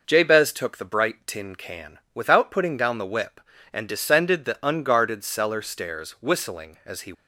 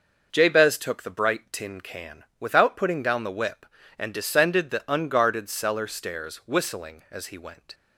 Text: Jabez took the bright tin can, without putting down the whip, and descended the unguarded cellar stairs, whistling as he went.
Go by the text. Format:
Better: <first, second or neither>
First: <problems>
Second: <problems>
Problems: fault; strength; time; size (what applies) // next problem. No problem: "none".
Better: second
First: stops before "went"; at 7.1 s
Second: none